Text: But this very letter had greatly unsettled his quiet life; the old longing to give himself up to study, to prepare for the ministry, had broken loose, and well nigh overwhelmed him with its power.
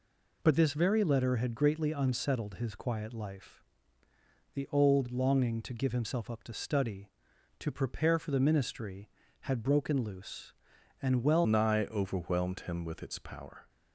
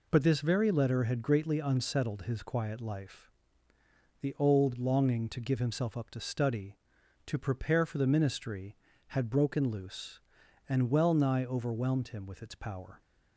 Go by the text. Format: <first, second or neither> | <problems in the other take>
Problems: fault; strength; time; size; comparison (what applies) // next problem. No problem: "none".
second | changes voice at "nigh"; from 11.4 s on; 2.2 s long